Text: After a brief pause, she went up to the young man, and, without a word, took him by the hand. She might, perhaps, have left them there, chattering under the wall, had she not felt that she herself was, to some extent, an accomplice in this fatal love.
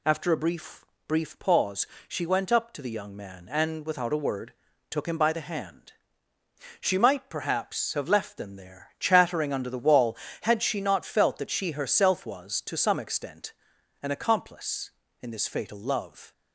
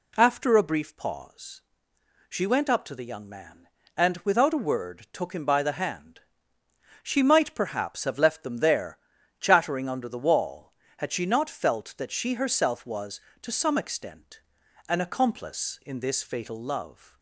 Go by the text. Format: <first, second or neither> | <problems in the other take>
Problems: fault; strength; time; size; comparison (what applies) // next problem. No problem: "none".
second | says "brief" twice; at 1.0 s